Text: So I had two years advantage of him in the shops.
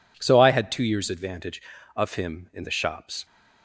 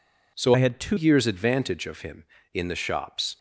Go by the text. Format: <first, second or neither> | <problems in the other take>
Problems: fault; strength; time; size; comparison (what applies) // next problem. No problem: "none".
first | changes voice from "I" to "two"; from 0.5 to 0.9 s; 0.4 s long